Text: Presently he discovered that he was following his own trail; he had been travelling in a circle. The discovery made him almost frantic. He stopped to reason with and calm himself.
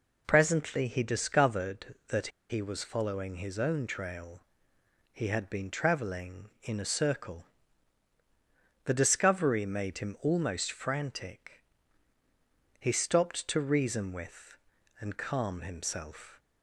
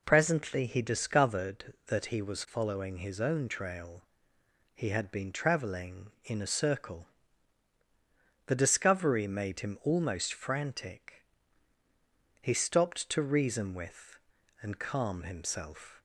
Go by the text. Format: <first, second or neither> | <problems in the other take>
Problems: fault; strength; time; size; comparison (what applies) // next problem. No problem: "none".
second | pauses between "that" and "he"; slight; at 2.2 s; 0.21 s long